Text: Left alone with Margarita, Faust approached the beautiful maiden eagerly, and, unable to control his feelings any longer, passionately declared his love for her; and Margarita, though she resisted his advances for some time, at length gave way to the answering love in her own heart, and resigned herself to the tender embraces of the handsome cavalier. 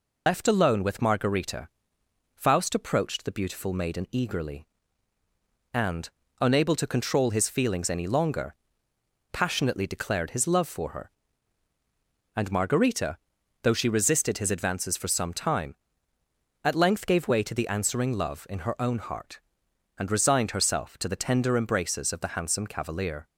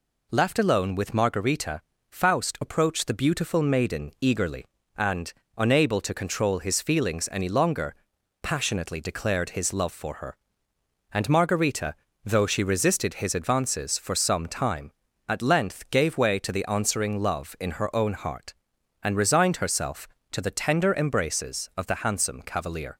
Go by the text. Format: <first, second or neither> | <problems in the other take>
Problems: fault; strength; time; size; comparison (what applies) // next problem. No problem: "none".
second | loses the start of "Left"; at 0.2 s; 80 ms